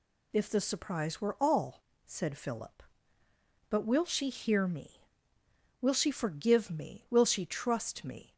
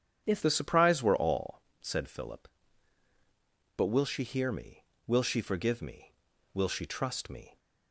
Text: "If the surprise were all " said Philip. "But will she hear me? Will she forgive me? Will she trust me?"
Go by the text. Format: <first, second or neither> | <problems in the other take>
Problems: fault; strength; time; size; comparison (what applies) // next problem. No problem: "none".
first | starts louder than the rest; strong; until 1.2 s; 8.5 dB // changes voice at "the"; from 0.4 s on; 7.1 s long